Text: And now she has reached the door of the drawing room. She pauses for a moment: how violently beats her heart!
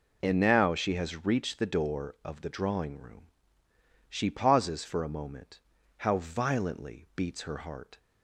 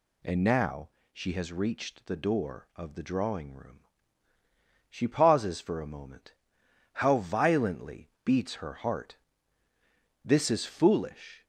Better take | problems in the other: first | pauses between "now" and "she"; slight; at 0.8 s; 0.22 s long // pauses between "violently" and "beats"; slight; at 8.0 s; 0.16 s long // goes on to say "This is foolish"; noticeable; from 10.2 s on; 1.2 s long

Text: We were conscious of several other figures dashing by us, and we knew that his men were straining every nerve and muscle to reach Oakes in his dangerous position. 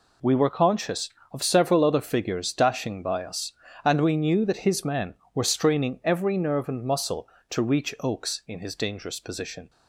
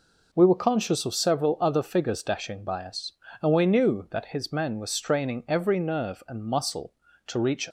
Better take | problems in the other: first | stops before "Oakes in his dangerous position"; at 7.6 s

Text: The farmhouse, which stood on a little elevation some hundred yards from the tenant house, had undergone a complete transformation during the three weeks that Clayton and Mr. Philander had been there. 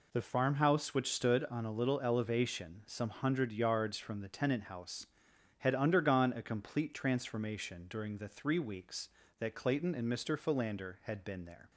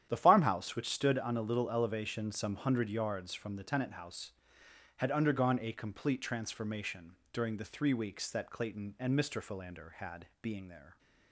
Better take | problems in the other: first | starts louder than the rest; strong; until 1.1 s; 10.5 dB // pauses between "transformation" and "during"; slight; at 7.1 s; 0.16 s long // says "being" for "been"; at 10.4 s

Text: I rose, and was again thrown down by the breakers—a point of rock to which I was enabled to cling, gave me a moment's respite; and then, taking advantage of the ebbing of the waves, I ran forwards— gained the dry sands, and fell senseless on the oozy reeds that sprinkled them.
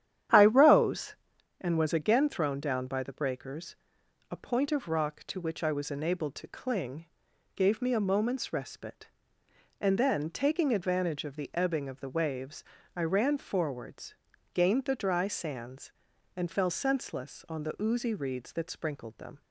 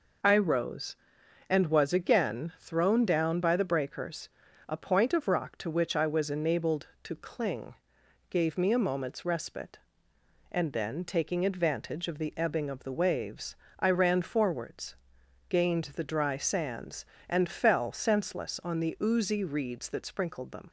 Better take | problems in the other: second | starts louder than the rest; strong; until 1.3 s; 10.5 dB

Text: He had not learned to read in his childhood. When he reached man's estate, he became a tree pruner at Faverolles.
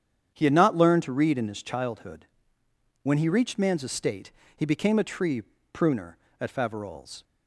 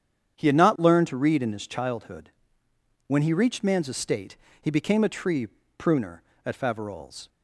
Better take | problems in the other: neither | starts louder than the rest; strong; the same in both // pauses between "tree" and "pruner"; slight; the same in both

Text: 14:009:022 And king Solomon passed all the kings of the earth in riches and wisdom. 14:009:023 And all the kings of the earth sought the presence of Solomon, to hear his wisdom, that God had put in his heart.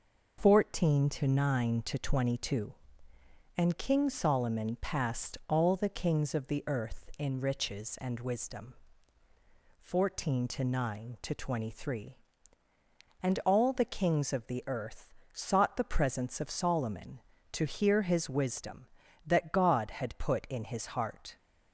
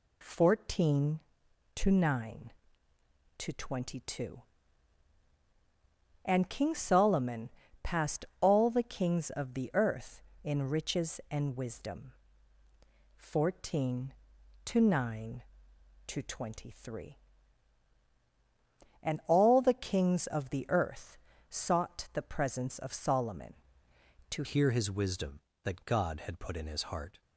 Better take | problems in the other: first | pauses between "Solomon" and "passed"; slight; at 7.4 s; 0.32 s long // pauses between "passed" and "all"; slight; at 8.2 s; 0.16 s long // pauses between "earth" and "sought"; slight; at 21.1 s; 0.32 s long; slight in the first // changes voice at "hear"; from 24.4 s on; 2.8 s long

